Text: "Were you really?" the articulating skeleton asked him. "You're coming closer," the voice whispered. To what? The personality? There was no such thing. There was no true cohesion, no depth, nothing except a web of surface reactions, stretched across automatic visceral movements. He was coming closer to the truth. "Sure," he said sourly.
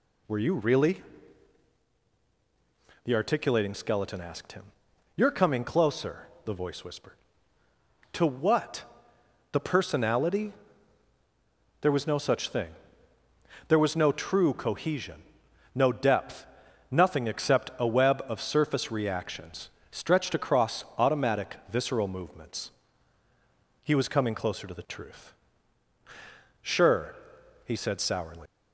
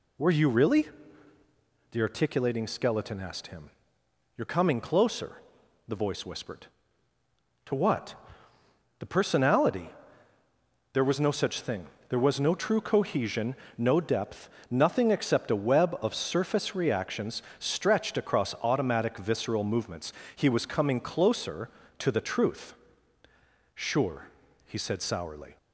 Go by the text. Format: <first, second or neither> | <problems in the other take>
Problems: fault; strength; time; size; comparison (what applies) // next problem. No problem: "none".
second | leaves "sourly" unfinished; at 28.4 s; 120 ms